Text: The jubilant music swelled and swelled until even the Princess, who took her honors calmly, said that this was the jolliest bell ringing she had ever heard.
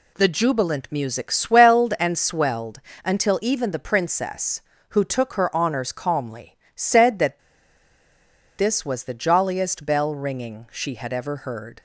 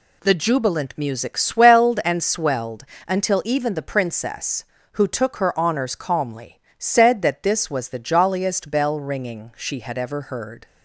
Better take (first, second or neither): second